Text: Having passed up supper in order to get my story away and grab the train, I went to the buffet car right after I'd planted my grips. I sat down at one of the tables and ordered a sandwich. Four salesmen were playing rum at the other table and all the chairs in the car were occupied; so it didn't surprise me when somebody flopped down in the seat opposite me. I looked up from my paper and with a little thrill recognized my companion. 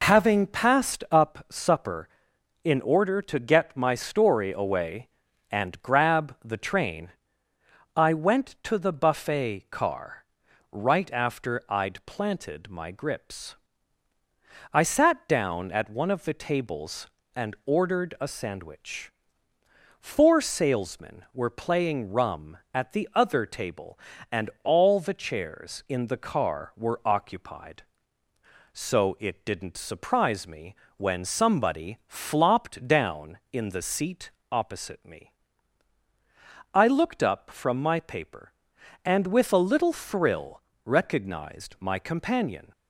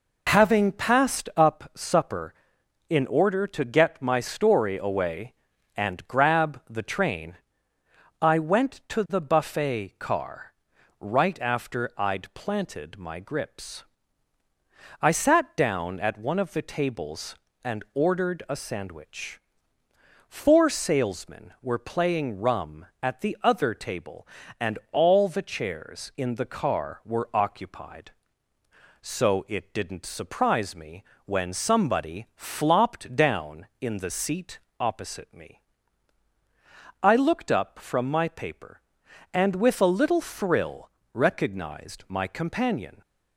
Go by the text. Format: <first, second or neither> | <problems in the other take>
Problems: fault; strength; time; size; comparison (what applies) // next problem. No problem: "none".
neither | pauses between "car" and "right"; noticeable; the same in both // pauses between "me" and "when"; slight; the same in both // pauses between "seat" and "opposite"; slight; the same in both // pauses between "thrill" and "recognized"; slight; the same in both